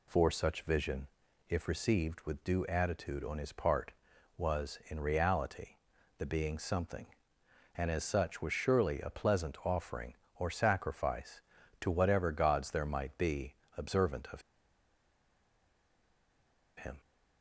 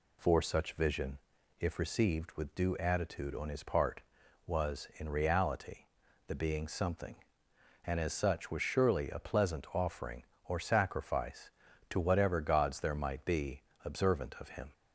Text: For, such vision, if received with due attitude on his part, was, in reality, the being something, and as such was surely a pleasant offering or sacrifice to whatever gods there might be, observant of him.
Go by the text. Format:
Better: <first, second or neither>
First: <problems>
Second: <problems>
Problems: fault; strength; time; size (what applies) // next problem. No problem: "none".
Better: second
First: pauses between "of" and "him"; strong; at 14.4 s; 2.3 s long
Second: none